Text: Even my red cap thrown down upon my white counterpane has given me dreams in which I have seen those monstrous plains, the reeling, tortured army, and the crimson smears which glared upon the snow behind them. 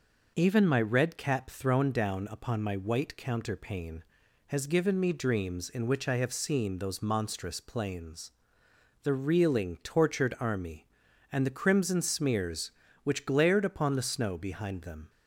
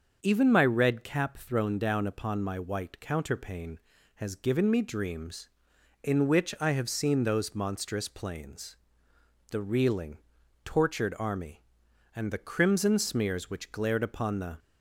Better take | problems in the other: first | starts louder than the rest; until 1.2 s; 6.5 dB // stops before "snow behind them"; at 14.5 s

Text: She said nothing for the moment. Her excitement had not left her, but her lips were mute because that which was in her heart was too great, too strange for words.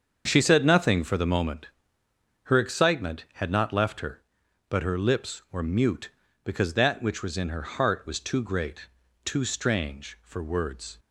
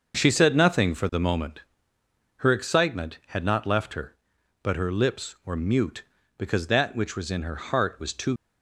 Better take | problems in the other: first | starts louder than the rest; until 1.1 s; 6.5 dB; also in the first // stops before "great too strange for words"; at 8.3 s

